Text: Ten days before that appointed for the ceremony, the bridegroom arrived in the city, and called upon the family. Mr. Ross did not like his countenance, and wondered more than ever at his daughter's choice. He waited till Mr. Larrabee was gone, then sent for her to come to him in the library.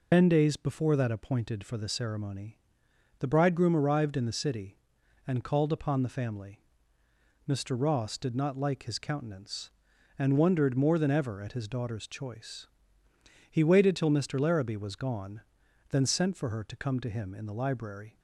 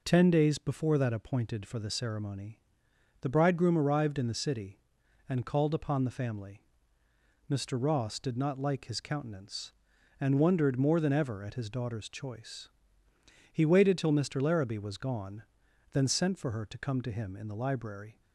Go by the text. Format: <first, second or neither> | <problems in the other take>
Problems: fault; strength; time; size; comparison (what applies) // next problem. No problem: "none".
second | loses the start of "Ten"; at 0.1 s; 90 ms